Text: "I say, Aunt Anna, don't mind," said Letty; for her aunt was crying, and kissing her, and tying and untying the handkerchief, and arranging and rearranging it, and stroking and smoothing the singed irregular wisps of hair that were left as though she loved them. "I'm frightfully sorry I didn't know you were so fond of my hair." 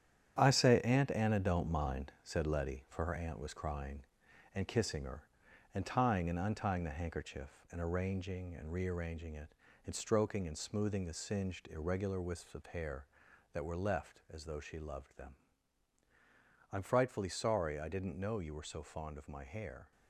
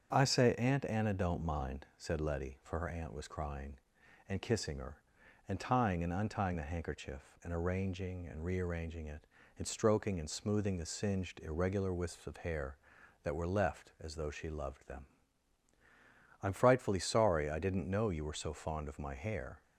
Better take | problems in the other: second | gets quieter; strong; throughout; 7.5 dB // starts louder than the rest; strong; until 1.4 s; 9.5 dB; strong in the second

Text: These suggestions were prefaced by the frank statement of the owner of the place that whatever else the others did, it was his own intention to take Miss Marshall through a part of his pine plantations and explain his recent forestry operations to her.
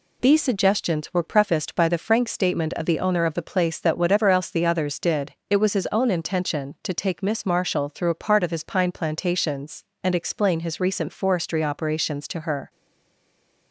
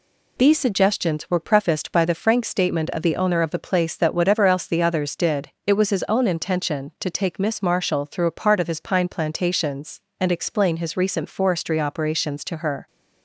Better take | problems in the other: second | stays silent after the last word; from 12.6 s on; 1.1 s long

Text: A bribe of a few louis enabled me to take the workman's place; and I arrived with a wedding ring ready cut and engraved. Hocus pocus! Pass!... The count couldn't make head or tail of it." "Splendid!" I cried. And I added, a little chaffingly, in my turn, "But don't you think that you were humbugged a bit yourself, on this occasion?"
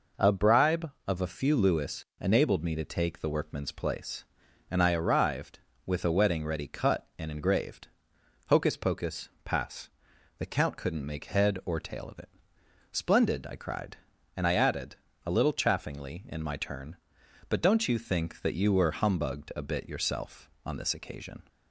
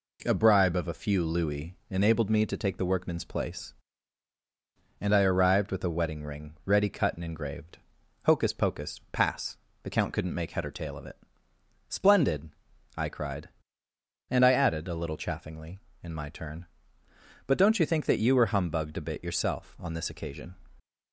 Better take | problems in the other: second | pauses between "louis" and "enabled"; slight; at 2.0 s; 0.16 s long; slight in the second // skips "ring"; at 6.4 s

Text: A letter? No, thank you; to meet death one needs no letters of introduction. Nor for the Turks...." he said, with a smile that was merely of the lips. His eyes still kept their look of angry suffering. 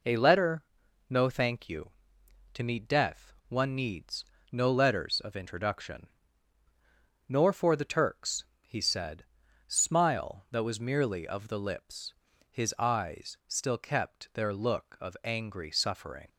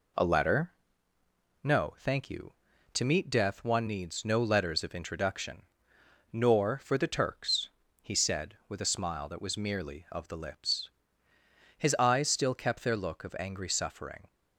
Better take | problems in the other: second | pauses between "death" and "one"; slight; at 3.3 s; 0.15 s long // pauses between "needs" and "no"; slight; at 4.2 s; 0.28 s long // skips "with a"; at 9.4 s

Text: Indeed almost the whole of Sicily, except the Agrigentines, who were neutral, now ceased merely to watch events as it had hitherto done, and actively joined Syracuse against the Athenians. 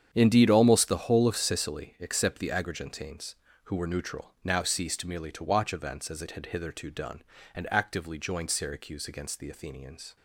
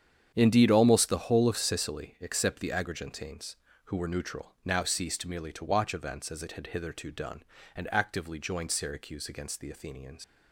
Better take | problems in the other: first | starts louder than the rest; strong; until 1.3 s; 8.5 dB; strong in the first // leaves "Athenians" unfinished; at 10.2 s; 120 ms

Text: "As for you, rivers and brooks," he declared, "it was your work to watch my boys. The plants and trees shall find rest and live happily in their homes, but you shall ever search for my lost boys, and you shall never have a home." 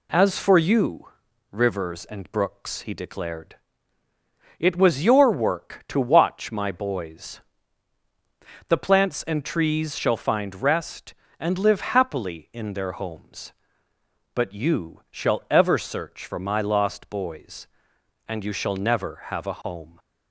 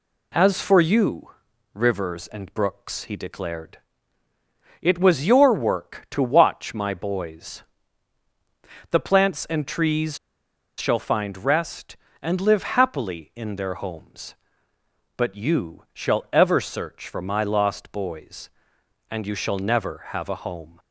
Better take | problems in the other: first | pauses between "trees" and "shall"; noticeable; at 10.1 s; 0.60 s long

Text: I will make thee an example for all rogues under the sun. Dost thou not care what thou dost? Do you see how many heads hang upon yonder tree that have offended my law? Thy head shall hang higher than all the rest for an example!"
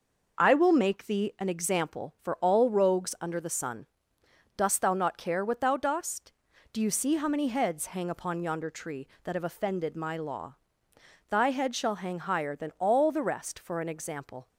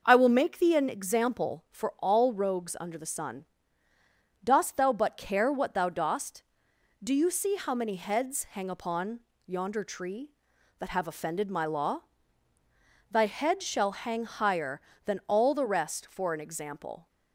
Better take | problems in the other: first | starts louder than the rest; noticeable; until 1.0 s; 6 dB // says "but" for "not"; at 4.9 s // pauses between "upon" and "yonder"; slight; at 9.2 s; 0.26 s long

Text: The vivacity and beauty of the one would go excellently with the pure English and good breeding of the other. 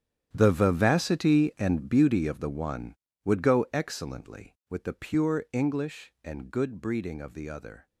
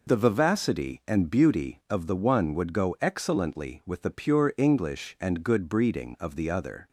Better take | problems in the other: second | gets quieter; strong; throughout; 15.5 dB

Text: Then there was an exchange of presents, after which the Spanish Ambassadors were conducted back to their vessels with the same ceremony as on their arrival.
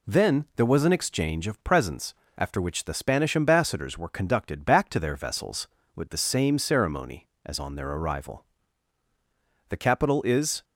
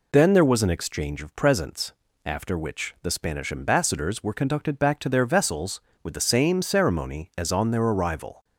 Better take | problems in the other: second | goes on to say "The capital is"; noticeable; from 9.6 s on; 0.94 s long

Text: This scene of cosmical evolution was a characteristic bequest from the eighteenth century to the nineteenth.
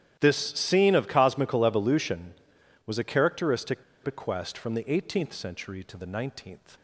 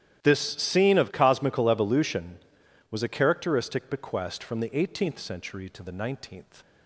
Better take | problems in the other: second | starts louder than the rest; strong; until 1.2 s; 11.5 dB; strong in the second // pauses between "characteristic" and "bequest"; slight; at 3.8 s; 0.20 s long

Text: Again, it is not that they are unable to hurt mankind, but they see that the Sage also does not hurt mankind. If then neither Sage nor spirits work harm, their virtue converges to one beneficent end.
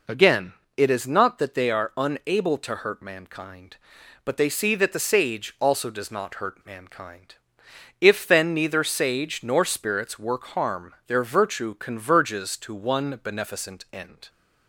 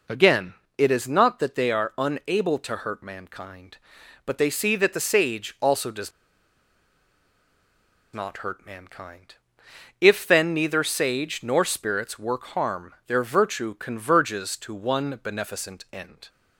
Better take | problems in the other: first | pauses between "does" and "not"; strong; at 6.1 s; 2.0 s long

